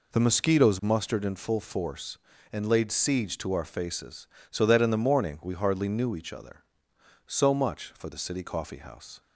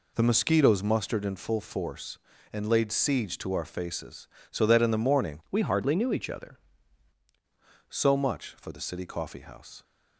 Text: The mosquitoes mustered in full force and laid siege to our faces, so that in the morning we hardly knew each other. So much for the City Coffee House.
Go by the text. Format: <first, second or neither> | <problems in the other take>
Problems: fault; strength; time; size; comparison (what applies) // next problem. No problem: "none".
first | changes voice from "we" to "other"; from 5.5 to 6.5 s; 1.0 s long